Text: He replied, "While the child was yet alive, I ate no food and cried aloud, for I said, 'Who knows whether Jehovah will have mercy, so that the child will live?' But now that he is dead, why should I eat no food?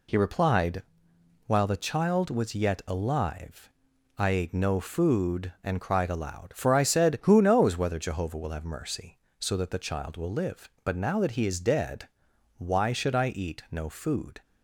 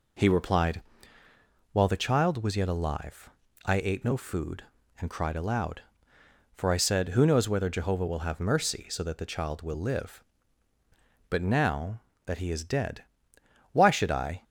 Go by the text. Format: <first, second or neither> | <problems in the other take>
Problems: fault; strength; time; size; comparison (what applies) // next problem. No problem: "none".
first | stops before "eat no food"; at 14.4 s